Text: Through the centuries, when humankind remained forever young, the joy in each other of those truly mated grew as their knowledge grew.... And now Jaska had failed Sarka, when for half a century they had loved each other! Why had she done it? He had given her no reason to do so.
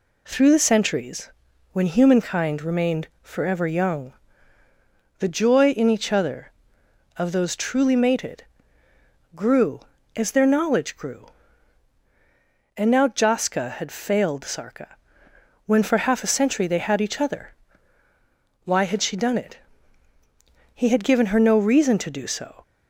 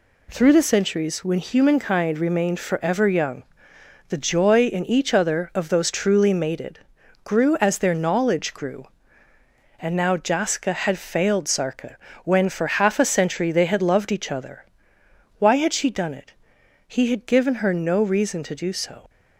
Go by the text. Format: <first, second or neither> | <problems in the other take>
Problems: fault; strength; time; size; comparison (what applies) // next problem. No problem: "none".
second | pauses between "mated" and "grew"; noticeable; at 8.4 s; 0.92 s long; noticeable in the second // skips "loved"; at 17.0 s